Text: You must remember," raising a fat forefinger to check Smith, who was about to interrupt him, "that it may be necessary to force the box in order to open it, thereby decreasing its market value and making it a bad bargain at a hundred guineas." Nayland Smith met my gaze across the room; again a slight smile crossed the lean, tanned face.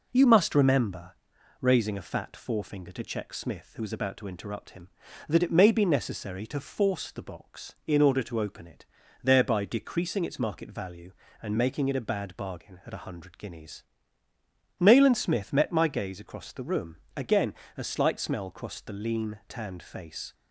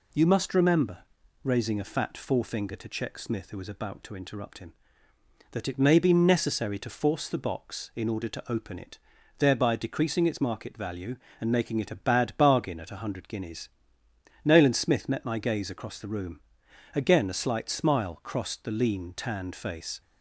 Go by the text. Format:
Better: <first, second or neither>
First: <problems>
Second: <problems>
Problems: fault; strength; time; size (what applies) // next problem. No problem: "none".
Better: second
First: pauses between "again" and "a"; slight; at 17.5 s; 0.22 s long // says "smell" for "smile"; at 18.1 s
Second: none